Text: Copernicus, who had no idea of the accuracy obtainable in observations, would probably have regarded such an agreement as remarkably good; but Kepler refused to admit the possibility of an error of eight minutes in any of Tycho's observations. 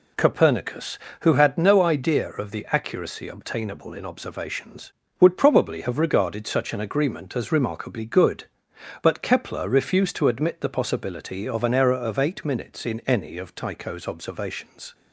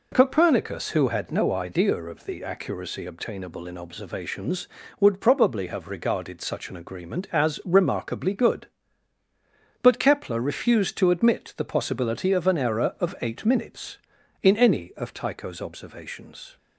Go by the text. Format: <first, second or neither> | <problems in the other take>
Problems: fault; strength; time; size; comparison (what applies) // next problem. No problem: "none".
neither | none